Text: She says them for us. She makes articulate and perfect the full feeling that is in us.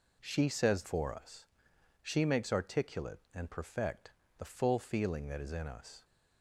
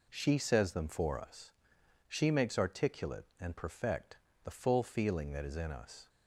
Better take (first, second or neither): second